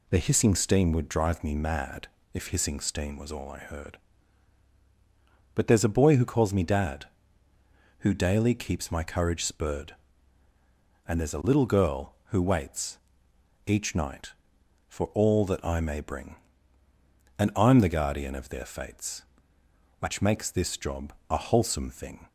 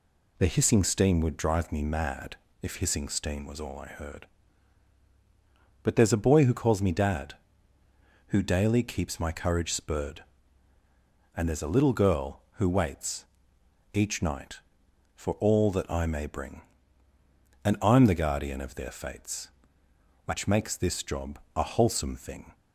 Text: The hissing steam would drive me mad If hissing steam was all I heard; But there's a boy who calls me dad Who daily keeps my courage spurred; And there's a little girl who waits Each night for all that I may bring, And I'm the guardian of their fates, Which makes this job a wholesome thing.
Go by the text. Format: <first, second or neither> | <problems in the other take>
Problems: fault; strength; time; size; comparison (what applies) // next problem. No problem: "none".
neither | pauses between "mad" and "If"; slight; the same in both // pauses between "waits" and "Each"; noticeable; the same in both // pauses between "job" and "a"; slight; the same in both